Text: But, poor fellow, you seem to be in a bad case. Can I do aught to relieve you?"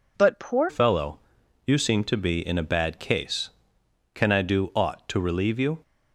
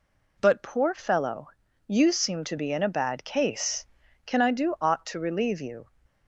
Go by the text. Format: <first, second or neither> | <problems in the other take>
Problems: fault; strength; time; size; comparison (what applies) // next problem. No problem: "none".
second | changes voice at "fellow"; from 0.6 s on; 5.2 s long